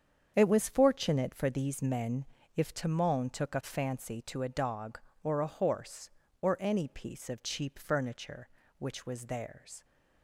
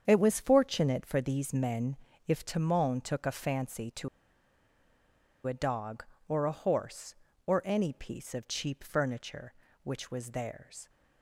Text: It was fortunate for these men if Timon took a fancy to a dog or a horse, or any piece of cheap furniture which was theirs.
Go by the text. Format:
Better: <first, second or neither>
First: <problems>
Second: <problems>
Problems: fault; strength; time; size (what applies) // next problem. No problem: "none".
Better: first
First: starts louder than the rest; strong; until 1.3 s; 7.5 dB // pauses between "men" and "if"; slight; at 2.2 s; 0.30 s long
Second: starts louder than the rest; strong; until 1.0 s; 7.5 dB // pauses between "men" and "if"; slight; at 1.9 s; 0.30 s long // pauses between "to" and "a"; strong; at 4.0 s; 1.3 s long